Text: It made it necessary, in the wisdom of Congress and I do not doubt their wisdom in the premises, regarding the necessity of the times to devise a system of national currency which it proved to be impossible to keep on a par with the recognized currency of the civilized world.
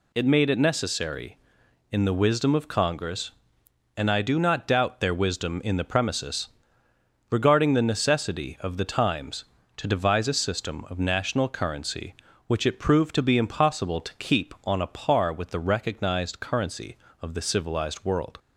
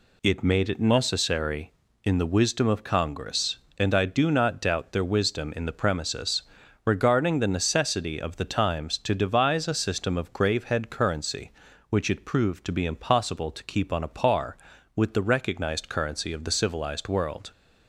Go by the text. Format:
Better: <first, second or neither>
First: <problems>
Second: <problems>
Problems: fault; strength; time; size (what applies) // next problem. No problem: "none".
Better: first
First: none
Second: says "gravehead" for "national"; at 10.3 s